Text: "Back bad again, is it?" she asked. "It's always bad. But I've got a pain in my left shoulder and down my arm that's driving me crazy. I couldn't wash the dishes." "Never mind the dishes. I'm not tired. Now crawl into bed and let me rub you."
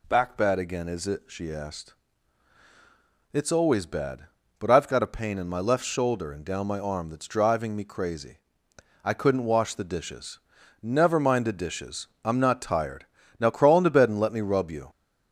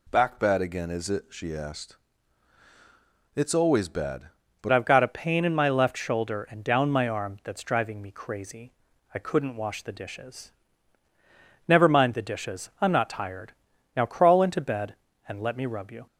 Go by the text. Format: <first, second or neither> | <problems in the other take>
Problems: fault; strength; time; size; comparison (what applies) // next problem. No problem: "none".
first | changes voice at "I've"; from 4.7 s on; 11.3 s long